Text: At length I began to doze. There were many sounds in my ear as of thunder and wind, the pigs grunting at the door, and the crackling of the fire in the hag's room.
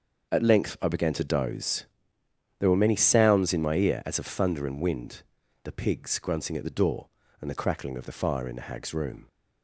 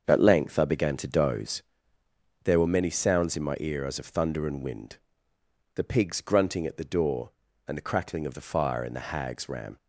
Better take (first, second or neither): first